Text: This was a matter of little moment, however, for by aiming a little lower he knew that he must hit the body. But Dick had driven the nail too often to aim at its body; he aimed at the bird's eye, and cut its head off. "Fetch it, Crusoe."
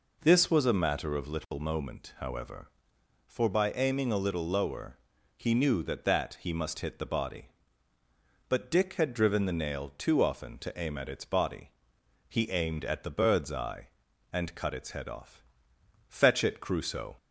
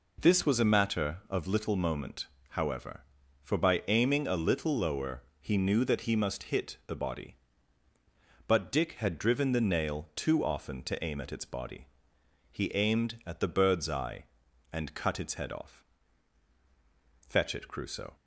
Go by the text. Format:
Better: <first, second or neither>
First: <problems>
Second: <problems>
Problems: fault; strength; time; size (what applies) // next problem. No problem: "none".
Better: second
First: pauses between "lower" and "he"; at 4.9 s; 0.40 s long // says "that" twice; at 6.0 s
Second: pauses between "lower" and "he"; slight; at 5.2 s; 0.18 s long